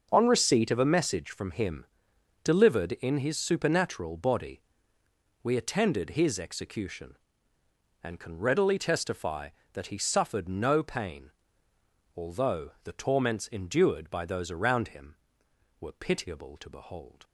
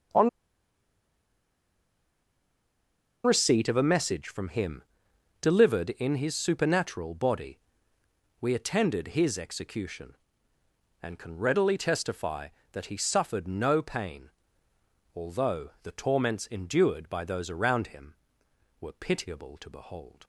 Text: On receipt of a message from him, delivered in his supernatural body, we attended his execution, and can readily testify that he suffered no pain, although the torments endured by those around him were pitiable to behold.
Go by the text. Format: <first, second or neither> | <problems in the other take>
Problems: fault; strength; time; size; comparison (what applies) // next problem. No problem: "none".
first | starts louder than the rest; until 4.0 s; 6.5 dB; also in the first // pauses between "On" and "receipt"; strong; at 0.2 s; 2.9 s long